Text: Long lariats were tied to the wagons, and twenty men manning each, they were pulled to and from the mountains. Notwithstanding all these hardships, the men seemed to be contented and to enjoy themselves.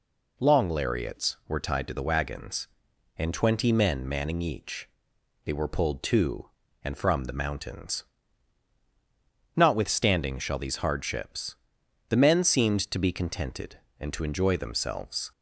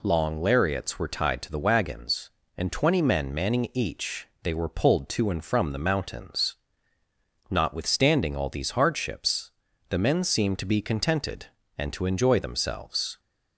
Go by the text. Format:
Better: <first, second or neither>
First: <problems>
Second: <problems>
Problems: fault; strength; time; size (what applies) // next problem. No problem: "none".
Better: second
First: says "shall" for "all"; at 10.3 s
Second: none